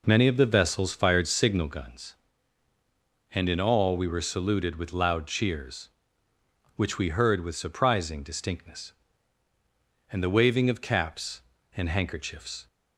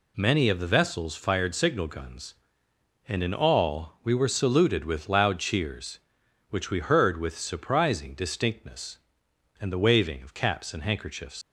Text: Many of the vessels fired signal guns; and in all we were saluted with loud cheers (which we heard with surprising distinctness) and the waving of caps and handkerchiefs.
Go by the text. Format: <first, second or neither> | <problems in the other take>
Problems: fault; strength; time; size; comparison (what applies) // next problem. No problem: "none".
first | leaves "handkerchiefs" unfinished; at 11.4 s; 130 ms